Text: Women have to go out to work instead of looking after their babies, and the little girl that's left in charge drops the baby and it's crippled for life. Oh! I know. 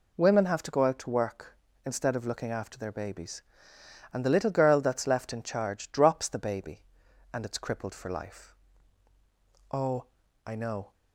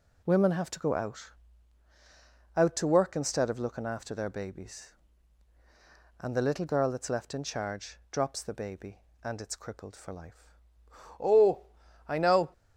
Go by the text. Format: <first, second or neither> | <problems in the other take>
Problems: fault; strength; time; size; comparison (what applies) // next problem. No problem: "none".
first | says "out" twice; at 2.5 s // pauses between "charge" and "drops"; slight; at 7.9 s; 0.16 s long